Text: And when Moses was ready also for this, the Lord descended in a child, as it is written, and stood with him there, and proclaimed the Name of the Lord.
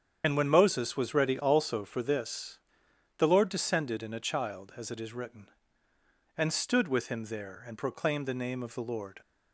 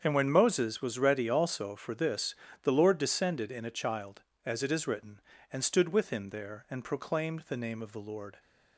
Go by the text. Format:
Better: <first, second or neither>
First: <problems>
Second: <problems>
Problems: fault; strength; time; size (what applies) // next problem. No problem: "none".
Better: second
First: loses the start of "And"; at 0.2 s; 40 ms // starts louder than the rest; strong; until 1.2 s; 8 dB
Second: starts louder than the rest; strong; until 1.0 s; 7 dB